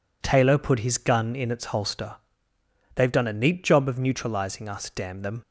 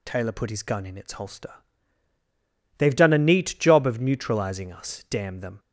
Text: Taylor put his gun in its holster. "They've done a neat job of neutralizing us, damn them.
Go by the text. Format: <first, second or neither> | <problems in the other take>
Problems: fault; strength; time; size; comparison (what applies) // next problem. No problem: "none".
neither | none